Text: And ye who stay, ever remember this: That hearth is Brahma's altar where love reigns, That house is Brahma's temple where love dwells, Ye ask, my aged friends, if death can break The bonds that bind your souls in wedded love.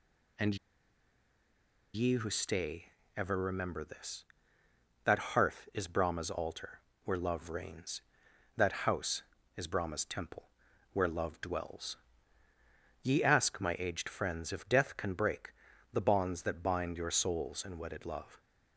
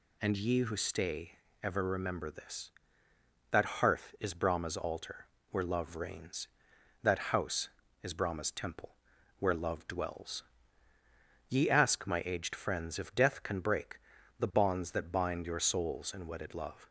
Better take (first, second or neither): second